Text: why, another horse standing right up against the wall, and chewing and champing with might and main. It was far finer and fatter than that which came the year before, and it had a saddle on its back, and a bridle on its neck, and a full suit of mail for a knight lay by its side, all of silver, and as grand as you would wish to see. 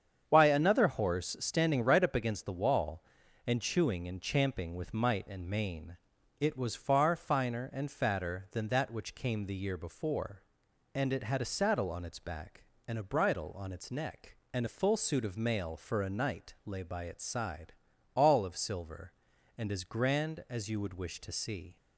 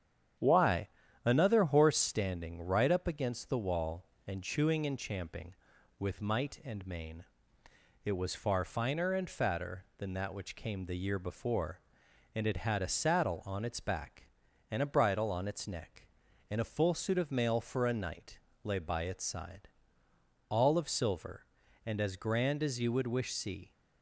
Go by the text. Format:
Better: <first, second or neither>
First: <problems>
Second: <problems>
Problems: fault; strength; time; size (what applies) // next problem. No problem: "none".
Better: first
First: starts louder than the rest; strong; until 1.2 s; 7.5 dB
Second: starts louder than the rest; strong; until 1.7 s; 9 dB // pauses between "knight" and "lay"; slight; at 18.3 s; 0.24 s long // skips "to"; at 23.3 s